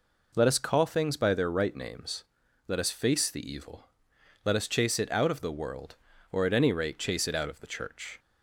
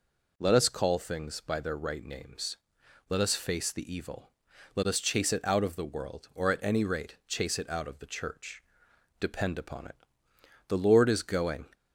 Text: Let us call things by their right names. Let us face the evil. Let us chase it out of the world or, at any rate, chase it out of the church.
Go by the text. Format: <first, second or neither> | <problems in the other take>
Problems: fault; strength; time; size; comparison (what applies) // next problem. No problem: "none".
first | goes on to say "Depend upon it the Lord is going"; strong; from 9.1 s on; 2.4 s long